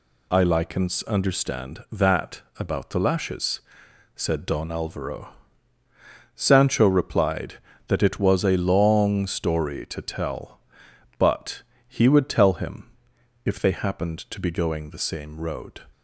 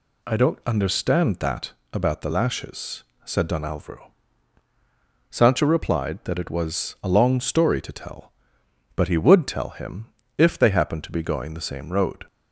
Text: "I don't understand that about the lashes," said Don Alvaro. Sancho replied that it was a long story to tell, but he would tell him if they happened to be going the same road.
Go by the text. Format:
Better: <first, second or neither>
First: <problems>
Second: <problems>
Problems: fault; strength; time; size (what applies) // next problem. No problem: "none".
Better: second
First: says "likens" for "don't"; at 0.4 s // pauses between "that" and "about"; slight; at 2.4 s; 0.18 s long // pauses between "but" and "he"; slight; at 11.6 s; 0.24 s long // pauses between "him" and "if"; noticeable; at 12.9 s; 0.54 s long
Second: pauses between "that" and "about"; slight; at 1.7 s; 0.20 s long // pauses between "him" and "if"; slight; at 10.0 s; 0.30 s long